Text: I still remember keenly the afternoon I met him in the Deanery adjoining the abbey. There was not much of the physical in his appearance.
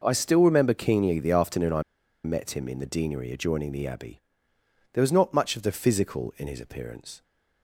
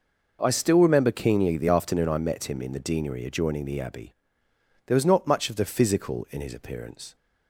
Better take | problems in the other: second | pauses between "I" and "met"; at 1.8 s; 0.41 s long

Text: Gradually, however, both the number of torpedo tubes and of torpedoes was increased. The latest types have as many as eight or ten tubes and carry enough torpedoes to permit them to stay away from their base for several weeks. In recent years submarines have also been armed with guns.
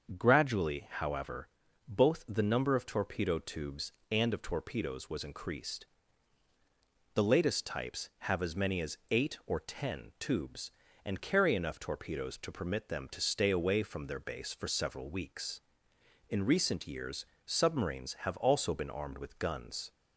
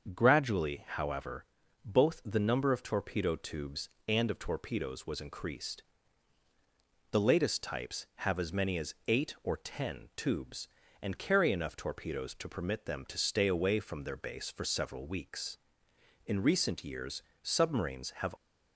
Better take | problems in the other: first | starts louder than the rest; until 1.1 s; 6.5 dB; also in the first // pauses between "years" and "submarines"; slight; at 17.2 s; 0.20 s long; slight in the first // stops before "also been armed with guns"; at 18.3 s

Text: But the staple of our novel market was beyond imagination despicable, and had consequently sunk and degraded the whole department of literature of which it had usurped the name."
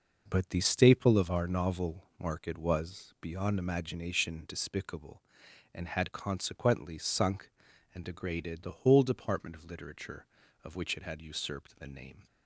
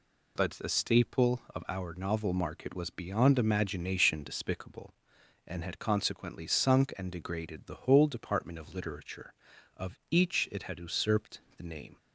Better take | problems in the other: first | says "each" for "which"; at 10.1 s // pauses between "usurped" and "the"; slight; at 11.4 s; 0.16 s long

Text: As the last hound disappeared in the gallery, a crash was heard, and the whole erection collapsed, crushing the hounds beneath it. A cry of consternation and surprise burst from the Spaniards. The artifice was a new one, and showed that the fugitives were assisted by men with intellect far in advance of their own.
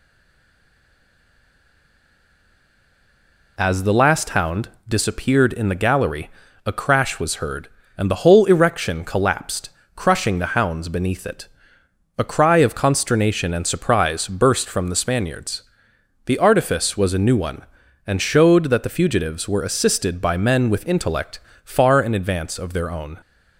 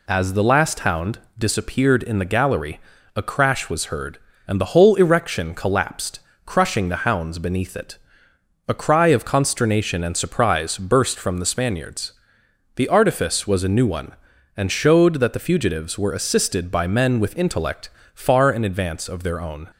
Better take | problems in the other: second | stays silent before the first word; strong; until 3.5 s; 3.5 s long // pauses between "hound" and "disappeared"; slight; at 4.6 s; 0.18 s long; slight in the second // pauses between "intellect" and "far"; slight; at 21.3 s; 0.26 s long; slight in the second

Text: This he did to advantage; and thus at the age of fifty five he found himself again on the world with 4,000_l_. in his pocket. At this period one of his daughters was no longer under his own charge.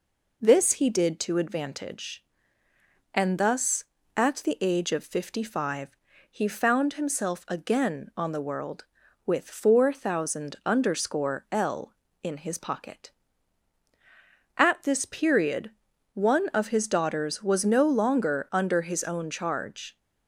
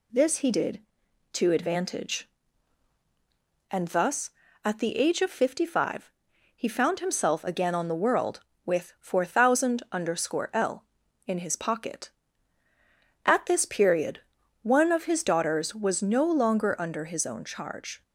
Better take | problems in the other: neither | pauses between "five" and "he"; the same in both // pauses between "period" and "one"; the same in both

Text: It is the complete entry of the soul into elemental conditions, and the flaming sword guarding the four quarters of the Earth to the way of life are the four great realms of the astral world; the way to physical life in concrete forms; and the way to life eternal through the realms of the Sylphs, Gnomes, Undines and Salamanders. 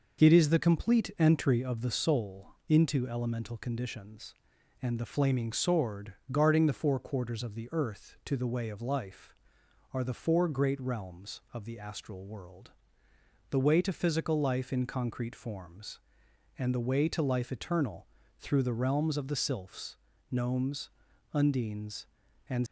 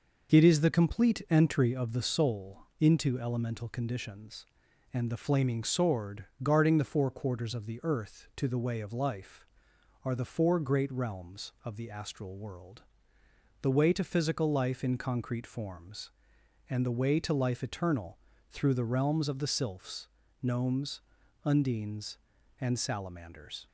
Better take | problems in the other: second | pauses between "soul" and "into"; slight; at 2.4 s; 0.18 s long; slight in the second // pauses between "sword" and "guarding"; slight; at 6.1 s; 0.16 s long; slight in the second // pauses between "eternal" and "through"; slight; at 18.0 s; 0.34 s long; slight in the second // stops before "Salamanders"; at 22.6 s

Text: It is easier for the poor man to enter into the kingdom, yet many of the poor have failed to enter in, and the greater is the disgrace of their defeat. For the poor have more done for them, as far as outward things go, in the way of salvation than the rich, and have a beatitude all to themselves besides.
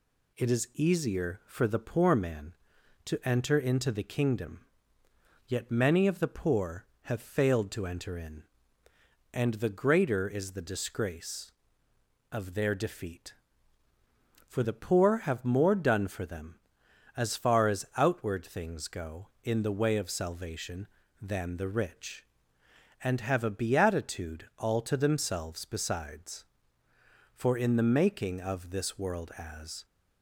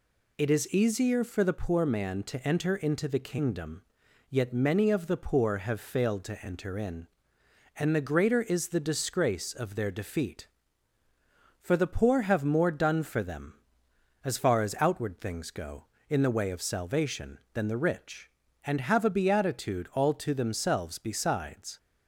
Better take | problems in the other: second | goes on to say "For in the making of this world as"; strong; from 27.3 s on; 2.5 s long

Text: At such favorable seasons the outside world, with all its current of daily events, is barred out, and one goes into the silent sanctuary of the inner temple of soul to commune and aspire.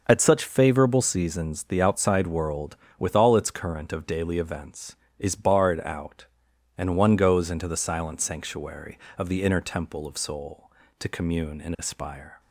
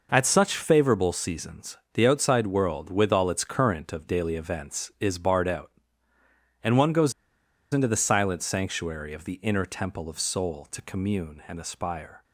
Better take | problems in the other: first | pauses between "seasons" and "the"; slight; at 1.7 s; 0.18 s long // pauses between "goes" and "into"; noticeable; at 7.1 s; 0.60 s long

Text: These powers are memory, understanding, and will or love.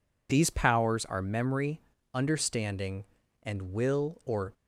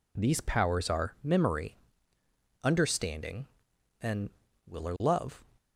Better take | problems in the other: second | stops before "love"; at 4.5 s

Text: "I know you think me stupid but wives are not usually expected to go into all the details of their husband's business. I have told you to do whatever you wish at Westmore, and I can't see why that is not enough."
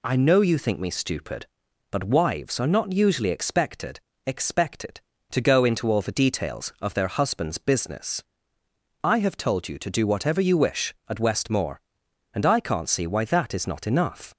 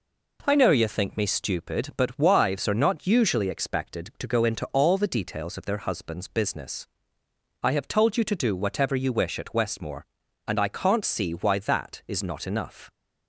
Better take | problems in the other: second | says "expected" twice; at 4.2 s

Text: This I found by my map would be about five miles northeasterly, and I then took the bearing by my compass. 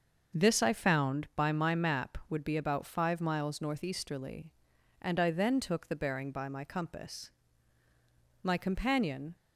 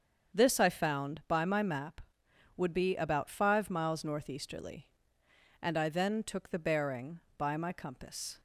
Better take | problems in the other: second | starts louder than the rest; until 1.4 s; 6.5 dB; strong in the second // goes on to say "My companion"; noticeable; from 8.4 s on; 0.94 s long

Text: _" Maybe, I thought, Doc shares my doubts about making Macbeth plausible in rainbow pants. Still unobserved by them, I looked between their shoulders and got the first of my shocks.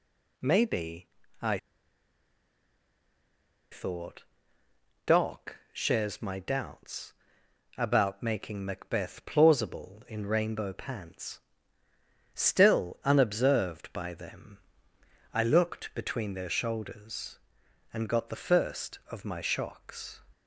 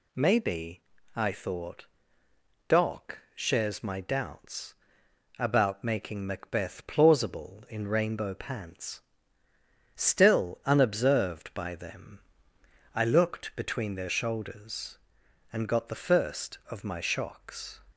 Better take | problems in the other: second | pauses between "I" and "thought"; strong; at 1.5 s; 2.1 s long // pauses between "Doc" and "shares"; slight; at 5.5 s; 0.16 s long; slight in the second // pauses between "doubts" and "about"; noticeable; at 7.1 s; 0.66 s long; noticeable in the second

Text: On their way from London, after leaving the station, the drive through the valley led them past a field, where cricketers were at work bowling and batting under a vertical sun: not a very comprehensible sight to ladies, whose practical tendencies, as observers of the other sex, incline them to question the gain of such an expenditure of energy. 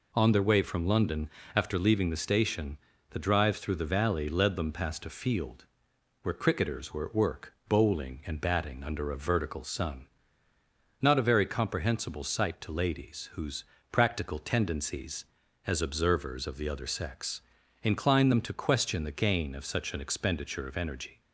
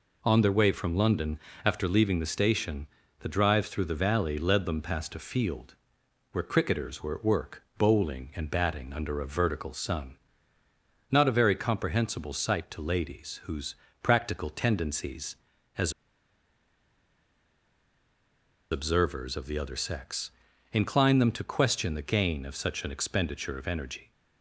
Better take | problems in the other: first | pauses between "whose" and "practical"; slight; at 13.7 s; 0.26 s long; slight in the first // pauses between "as" and "observers"; strong; at 15.9 s; 2.7 s long

